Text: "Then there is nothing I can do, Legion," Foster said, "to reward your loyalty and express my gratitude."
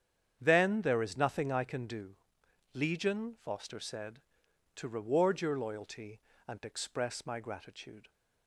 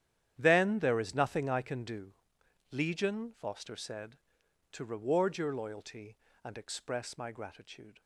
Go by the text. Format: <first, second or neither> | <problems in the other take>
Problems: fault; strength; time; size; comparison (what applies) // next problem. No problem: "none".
first | gets quieter; strong; throughout; 15 dB // starts louder than the rest; strong; until 1.3 s; 10 dB; strong in the first